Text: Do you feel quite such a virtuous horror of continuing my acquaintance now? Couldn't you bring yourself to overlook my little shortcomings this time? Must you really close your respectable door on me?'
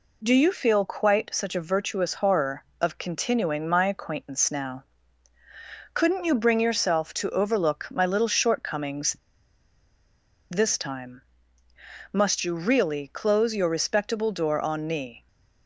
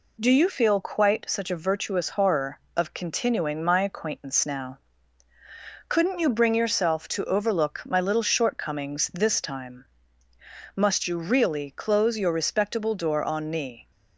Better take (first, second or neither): second